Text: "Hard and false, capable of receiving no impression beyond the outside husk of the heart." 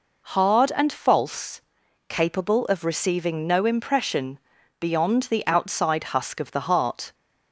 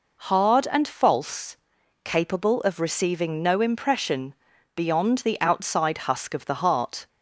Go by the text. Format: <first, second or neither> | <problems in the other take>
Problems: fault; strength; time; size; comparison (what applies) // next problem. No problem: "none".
neither | pauses between "impression" and "beyond"; the same in both